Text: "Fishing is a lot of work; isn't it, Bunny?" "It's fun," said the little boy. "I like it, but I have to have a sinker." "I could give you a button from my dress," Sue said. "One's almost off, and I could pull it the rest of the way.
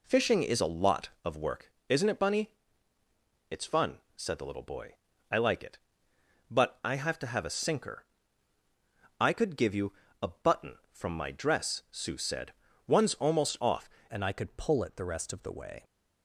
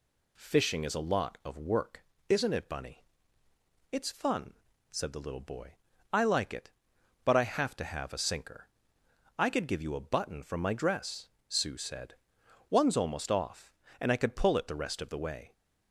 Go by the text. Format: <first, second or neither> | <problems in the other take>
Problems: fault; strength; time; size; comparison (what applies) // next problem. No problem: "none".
second | pauses between "you" and "a"; slight; at 9.9 s; 0.28 s long // changes voice at "and"; from 14.0 s on; 1.8 s long